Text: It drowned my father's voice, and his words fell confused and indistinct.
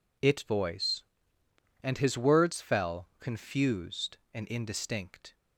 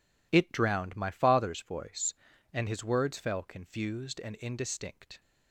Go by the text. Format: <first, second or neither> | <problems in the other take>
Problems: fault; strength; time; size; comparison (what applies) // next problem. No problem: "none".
second | skips "drowned my father's"; at 0.4 s